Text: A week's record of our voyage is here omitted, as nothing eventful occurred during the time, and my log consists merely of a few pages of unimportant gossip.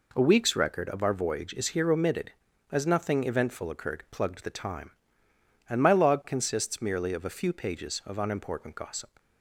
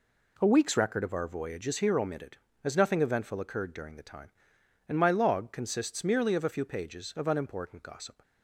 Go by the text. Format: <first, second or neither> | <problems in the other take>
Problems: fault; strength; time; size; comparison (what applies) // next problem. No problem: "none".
second | says "plugged" for "during"; at 4.0 s